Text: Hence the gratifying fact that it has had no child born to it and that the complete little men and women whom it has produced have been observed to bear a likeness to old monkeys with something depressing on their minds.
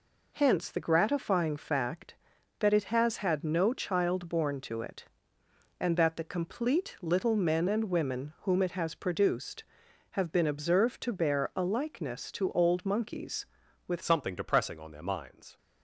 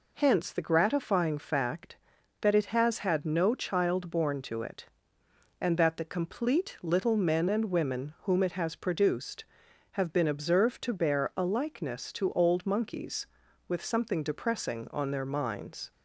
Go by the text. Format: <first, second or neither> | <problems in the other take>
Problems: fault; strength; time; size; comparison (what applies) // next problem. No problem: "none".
second | changes voice at "something"; from 14.0 s on; 1.5 s long